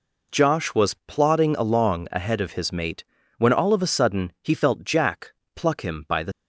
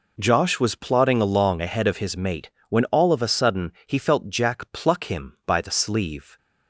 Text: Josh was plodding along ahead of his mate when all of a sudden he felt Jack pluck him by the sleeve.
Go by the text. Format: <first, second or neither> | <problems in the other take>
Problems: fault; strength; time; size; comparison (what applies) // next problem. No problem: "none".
second | pauses between "mate" and "when"; slight; at 3.0 s; 0.34 s long; slight in the second // pauses between "Jack" and "pluck"; slight; at 5.3 s; 0.24 s long // stops before "sleeve"; at 6.3 s